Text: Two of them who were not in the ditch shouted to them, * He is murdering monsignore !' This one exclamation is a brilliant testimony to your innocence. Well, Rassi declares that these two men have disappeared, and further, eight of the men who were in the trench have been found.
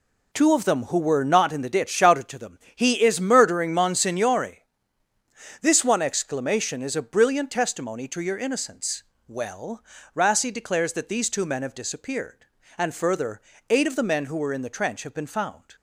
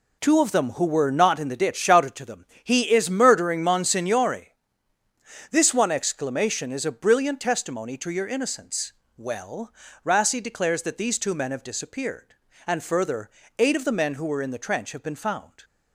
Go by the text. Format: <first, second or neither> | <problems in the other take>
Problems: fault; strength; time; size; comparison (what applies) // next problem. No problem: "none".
neither | none